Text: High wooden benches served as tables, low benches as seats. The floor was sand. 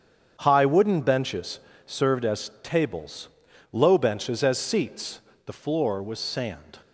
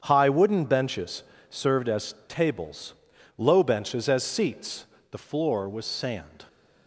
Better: neither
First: starts louder than the rest; strong; until 1.4 s; 8 dB // pauses between "benches" and "served"; slight; at 1.5 s; 0.28 s long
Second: starts louder than the rest; strong; until 1.0 s; 8 dB // pauses between "benches" and "served"; slight; at 1.2 s; 0.28 s long

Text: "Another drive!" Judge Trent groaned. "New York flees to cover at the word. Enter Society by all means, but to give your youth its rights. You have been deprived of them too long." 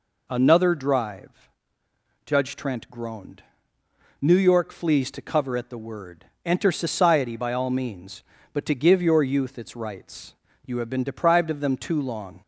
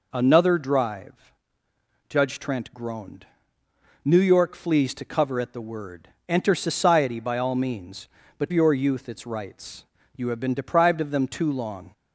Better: first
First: none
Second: skips "to give"; at 8.5 s

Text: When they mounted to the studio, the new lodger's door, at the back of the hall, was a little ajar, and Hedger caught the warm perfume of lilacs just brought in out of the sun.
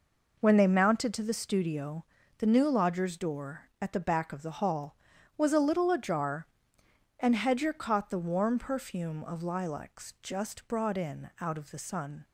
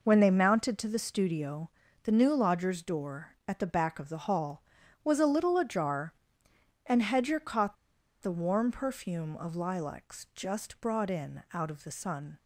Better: first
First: none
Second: pauses between "caught" and "the"; noticeable; at 7.7 s; 0.47 s long

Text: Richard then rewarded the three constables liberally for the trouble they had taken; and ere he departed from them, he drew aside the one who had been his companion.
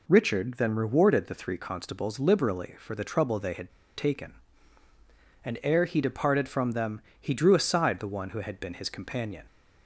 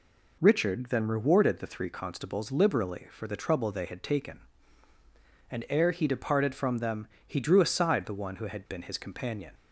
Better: second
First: pauses between "had" and "taken"; slight; at 3.6 s; 0.26 s long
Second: none

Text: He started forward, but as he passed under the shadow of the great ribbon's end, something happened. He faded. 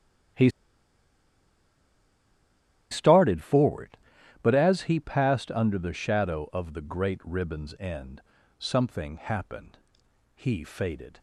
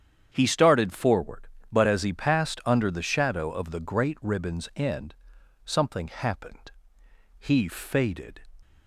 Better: second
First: starts louder than the rest; strong; until 3.7 s; 12 dB // pauses between "He" and "started"; strong; at 0.4 s; 2.4 s long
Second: starts louder than the rest; strong; until 1.3 s; 8.5 dB

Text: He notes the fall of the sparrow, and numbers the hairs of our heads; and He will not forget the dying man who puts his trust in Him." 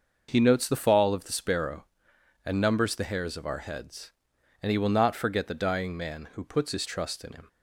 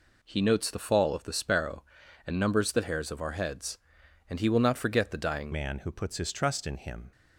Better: first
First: none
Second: changes voice at "man"; from 5.5 s on; 1.6 s long

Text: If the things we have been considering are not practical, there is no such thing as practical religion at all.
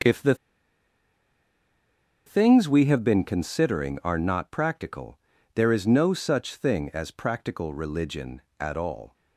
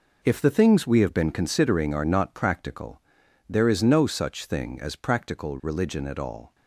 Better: second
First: pauses between "the" and "things"; strong; at 0.3 s; 1.9 s long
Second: none

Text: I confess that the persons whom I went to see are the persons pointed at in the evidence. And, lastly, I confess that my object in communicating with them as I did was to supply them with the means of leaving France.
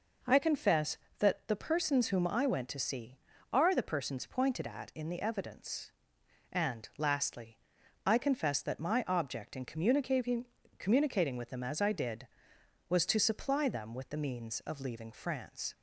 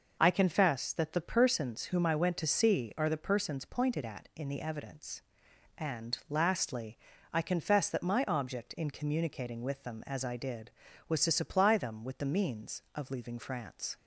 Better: second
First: says "communicating" twice; at 10.7 s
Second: none

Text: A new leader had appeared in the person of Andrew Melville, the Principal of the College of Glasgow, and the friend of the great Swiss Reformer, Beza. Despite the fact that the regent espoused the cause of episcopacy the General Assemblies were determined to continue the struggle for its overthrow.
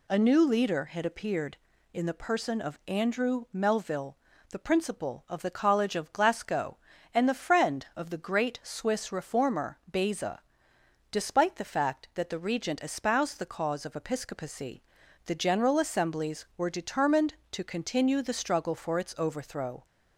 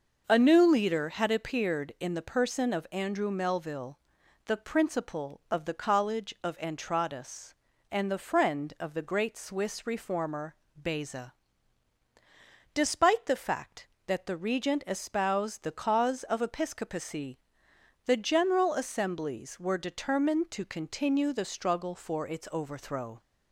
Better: first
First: pauses between "episcopacy" and "the"; at 14.8 s; 0.44 s long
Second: says "Entradas" for "Glasgow"; at 6.5 s // pauses between "episcopacy" and "the"; noticeable; at 17.3 s; 0.68 s long

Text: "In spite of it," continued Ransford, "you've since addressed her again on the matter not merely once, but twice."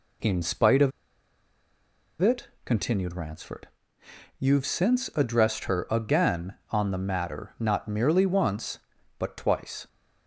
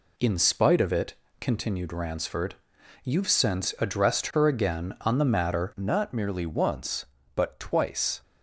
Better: second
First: pauses between "of" and "it"; strong; at 0.9 s; 1.3 s long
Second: none

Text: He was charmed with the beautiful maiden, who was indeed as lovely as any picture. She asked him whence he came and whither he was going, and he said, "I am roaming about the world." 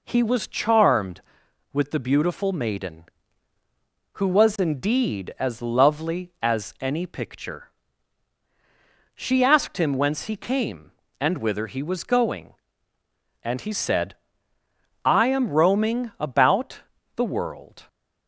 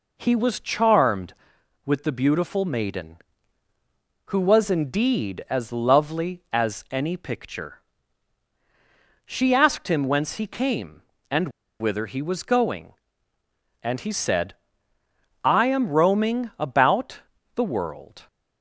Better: first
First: pauses between "about" and "the"; slight; at 16.7 s; 0.36 s long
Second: pauses between "and" and "whither"; slight; at 11.4 s; 0.30 s long // pauses between "about" and "the"; slight; at 17.1 s; 0.36 s long

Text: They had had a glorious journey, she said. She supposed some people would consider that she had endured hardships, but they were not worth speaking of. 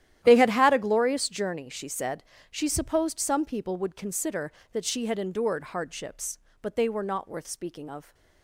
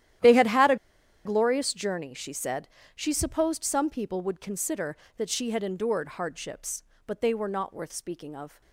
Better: first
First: starts louder than the rest; strong; until 1.2 s; 12 dB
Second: starts louder than the rest; strong; until 1.7 s; 12 dB // pauses between "a" and "glorious"; noticeable; at 0.7 s; 0.49 s long

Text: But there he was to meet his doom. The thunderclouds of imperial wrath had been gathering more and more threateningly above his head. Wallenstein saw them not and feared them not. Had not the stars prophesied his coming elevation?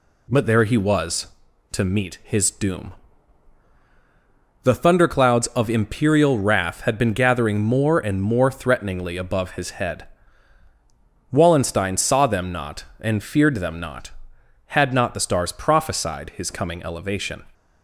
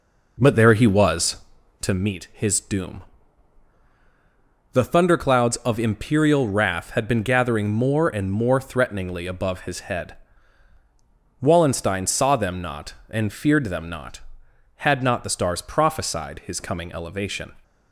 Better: first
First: none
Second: starts louder than the rest; noticeable; until 2.0 s; 4.5 dB

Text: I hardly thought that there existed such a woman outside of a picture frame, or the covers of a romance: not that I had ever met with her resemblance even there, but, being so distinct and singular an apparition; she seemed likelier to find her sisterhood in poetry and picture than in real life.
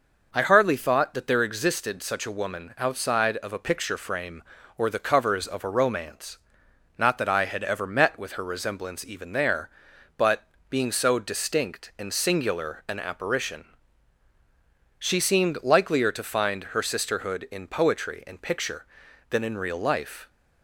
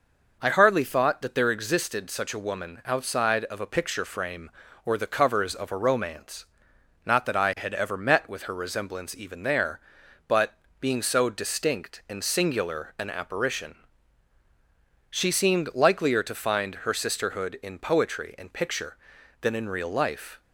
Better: neither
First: none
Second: none

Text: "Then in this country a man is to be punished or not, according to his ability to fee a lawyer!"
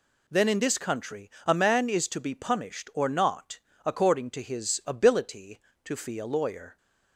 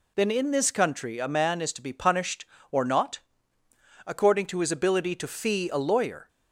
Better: neither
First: none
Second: none

